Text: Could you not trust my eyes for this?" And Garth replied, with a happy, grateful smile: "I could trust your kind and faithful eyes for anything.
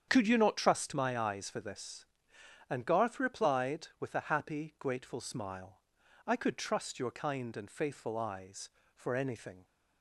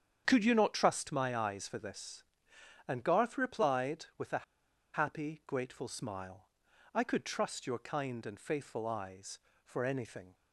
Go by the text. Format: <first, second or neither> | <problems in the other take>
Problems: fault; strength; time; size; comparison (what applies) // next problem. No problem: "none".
first | starts louder than the rest; strong; until 1.2 s; 8.5 dB; strong in the first // pauses between "a" and "happy"; noticeable; at 4.4 s; 0.52 s long